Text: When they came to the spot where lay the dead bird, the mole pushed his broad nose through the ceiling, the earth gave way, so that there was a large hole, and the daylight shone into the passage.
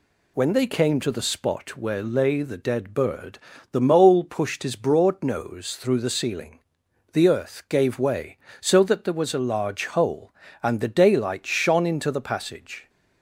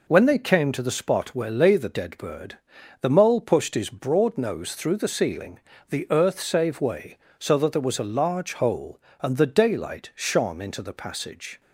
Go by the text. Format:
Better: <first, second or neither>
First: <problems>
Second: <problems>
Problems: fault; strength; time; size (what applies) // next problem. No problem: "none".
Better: first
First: none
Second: says "save" for "gave"; at 6.3 s